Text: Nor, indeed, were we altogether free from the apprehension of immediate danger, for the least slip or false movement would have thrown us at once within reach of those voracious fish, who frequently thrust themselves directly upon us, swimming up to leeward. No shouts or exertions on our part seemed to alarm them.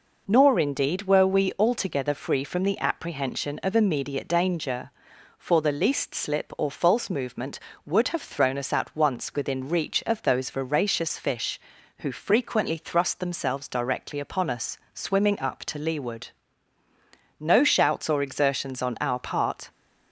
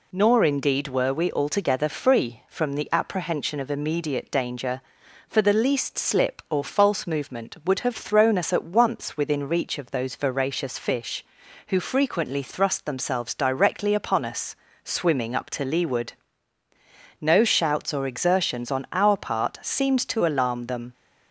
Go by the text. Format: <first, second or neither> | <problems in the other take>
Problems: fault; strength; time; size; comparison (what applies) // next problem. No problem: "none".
second | stops before "seemed to alarm them"; at 19.7 s